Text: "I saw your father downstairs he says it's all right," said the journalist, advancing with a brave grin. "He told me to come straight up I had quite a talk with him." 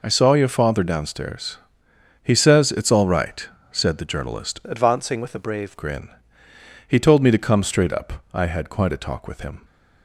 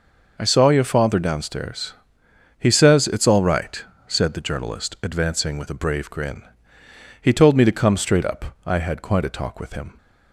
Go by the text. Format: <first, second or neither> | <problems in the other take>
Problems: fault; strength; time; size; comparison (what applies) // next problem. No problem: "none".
second | pauses between "downstairs" and "he"; noticeable; at 1.5 s; 0.64 s long; noticeable in the second // changes voice from "advancing" to "brave"; from 4.6 to 5.7 s; 1.1 s long